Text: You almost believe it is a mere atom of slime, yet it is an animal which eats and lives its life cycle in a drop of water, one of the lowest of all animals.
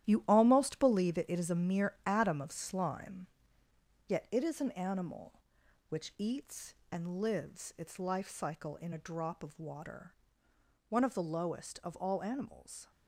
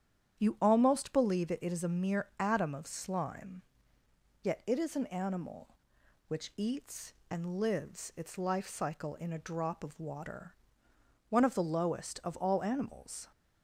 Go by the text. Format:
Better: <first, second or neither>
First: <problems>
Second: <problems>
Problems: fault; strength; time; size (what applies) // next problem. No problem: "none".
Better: second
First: gets quieter; strong; throughout; 9.5 dB // starts louder than the rest; strong; until 1.1 s; 12 dB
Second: starts louder than the rest; strong; until 1.4 s; 9 dB